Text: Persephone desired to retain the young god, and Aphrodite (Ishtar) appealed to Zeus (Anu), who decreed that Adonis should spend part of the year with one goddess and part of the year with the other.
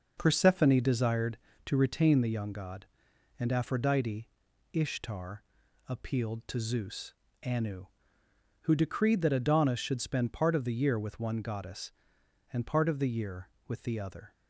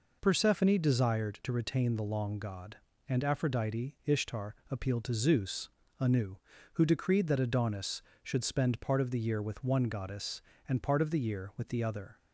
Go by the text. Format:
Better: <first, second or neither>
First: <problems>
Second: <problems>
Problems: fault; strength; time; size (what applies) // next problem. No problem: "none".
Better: first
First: none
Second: says "long" for "young"; at 2.0 s